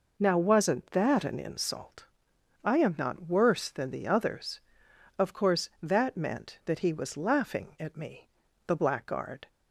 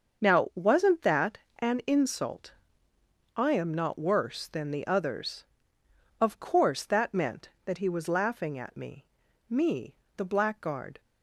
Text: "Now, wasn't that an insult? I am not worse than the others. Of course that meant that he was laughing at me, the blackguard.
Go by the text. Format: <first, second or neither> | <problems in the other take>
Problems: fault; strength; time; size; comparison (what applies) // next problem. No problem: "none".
first | starts louder than the rest; until 1.2 s; 6.5 dB // pauses between "that" and "an"; slight; at 1.3 s; 0.18 s long // says "me" twice; at 9.4 s